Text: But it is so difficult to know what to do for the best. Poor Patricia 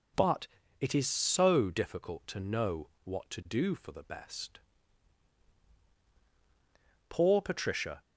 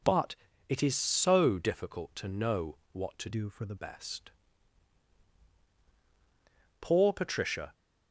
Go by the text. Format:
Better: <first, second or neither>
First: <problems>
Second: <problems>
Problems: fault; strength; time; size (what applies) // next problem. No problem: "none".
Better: first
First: pauses between "But" and "it"; slight; at 0.4 s; 0.32 s long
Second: pauses between "But" and "it"; slight; at 0.3 s; 0.32 s long // changes voice from "do" to "the"; from 3.3 to 3.7 s; 0.4 s long